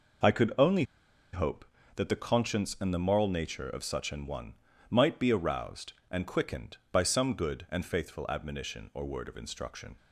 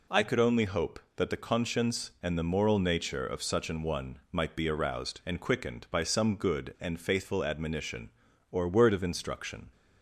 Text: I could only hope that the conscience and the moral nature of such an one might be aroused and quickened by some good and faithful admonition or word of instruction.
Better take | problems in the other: second | pauses between "only" and "hope"; noticeable; at 0.8 s; 0.49 s long // pauses between "one" and "might"; at 4.5 s; 0.38 s long

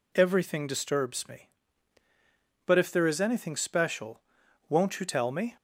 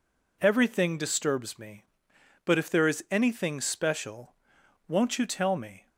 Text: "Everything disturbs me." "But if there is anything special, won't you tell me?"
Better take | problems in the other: neither | none

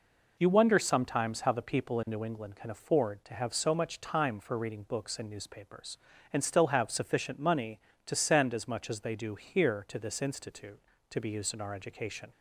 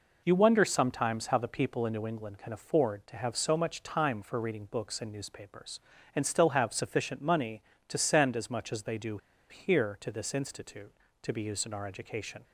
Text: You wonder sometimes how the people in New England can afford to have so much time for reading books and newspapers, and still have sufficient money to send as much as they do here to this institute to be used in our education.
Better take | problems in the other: first | pauses between "do" and "here"; slight; at 9.1 s; 0.32 s long

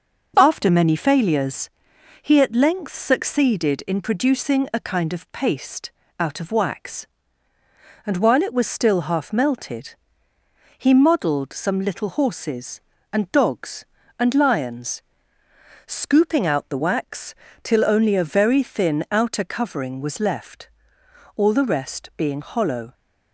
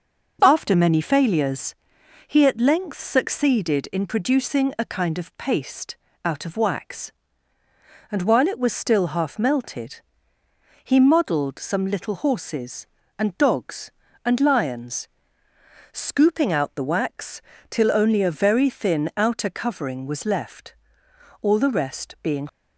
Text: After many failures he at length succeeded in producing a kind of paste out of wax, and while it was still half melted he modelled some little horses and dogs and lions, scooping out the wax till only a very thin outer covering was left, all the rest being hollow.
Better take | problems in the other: first | starts louder than the rest; until 1.4 s; 6.5 dB; noticeable in the first // pauses between "failures" and "he"; noticeable; at 1.7 s; 0.52 s long; noticeable in the first // pauses between "paste" and "out"; slight; at 5.9 s; 0.28 s long; slight in the first // pauses between "melted" and "he"; noticeable; at 10.0 s; 0.82 s long; noticeable in the first // pauses between "wax" and "till"; slight; at 17.4 s; 0.26 s long; slight in the first // stops before "hollow"; at 22.4 s

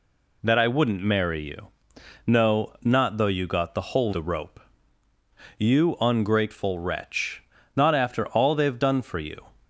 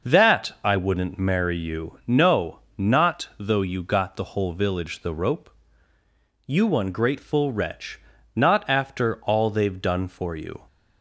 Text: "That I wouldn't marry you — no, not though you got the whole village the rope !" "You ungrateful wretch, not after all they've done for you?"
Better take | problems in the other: second | skips "village"; at 4.1 s

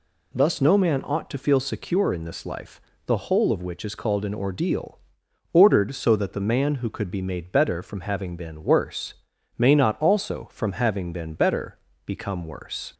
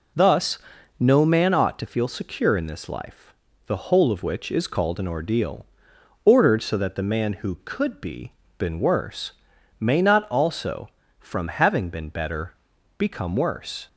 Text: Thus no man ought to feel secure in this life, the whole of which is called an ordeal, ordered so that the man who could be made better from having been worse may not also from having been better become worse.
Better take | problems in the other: first | pauses between "Thus" and "no"; at 0.5 s; 0.42 s long // skips "made better from having"; at 8.4 s // pauses between "worse" and "may"; noticeable; at 9.3 s; 0.48 s long; also in the first // pauses between "better" and "become"; at 12.5 s; 0.44 s long; slight in the first

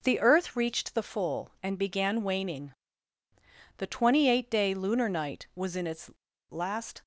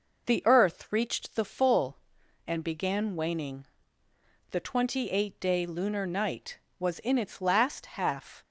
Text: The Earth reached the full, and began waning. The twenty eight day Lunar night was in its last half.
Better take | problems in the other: second | pauses between "its" and "last"; at 6.1 s; 0.38 s long // stops before "half"; at 7.0 s

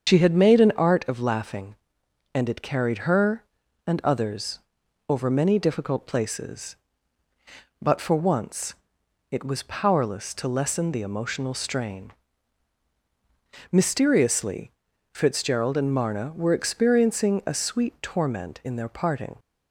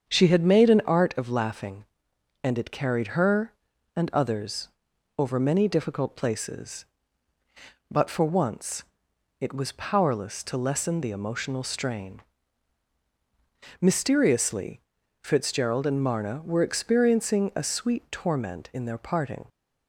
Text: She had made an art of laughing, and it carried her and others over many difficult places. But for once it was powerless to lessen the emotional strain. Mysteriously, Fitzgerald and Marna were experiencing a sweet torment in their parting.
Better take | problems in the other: second | loses the start of "She"; at 0.0 s; 80 ms // starts louder than the rest; strong; until 1.1 s; 7 dB; strong in the second // pauses between "others" and "over"; noticeable; at 4.5 s; 0.50 s long; noticeable in the second // pauses between "once" and "it"; noticeable; at 8.7 s; 0.56 s long; noticeable in the second

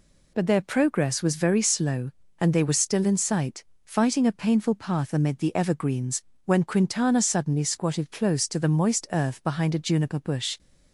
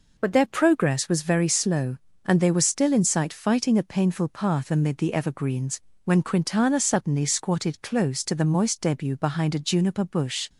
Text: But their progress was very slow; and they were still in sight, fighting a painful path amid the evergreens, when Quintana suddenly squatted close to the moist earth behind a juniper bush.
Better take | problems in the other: first | says "debut" for "earth"; at 8.8 s

